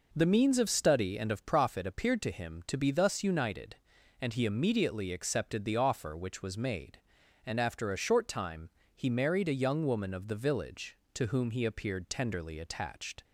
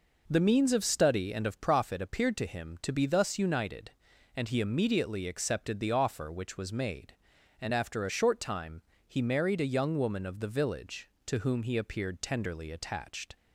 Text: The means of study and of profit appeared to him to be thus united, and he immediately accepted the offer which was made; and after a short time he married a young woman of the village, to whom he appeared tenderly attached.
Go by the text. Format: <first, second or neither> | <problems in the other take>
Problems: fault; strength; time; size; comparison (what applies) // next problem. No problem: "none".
neither | pauses between "time" and "he"; slight; the same in both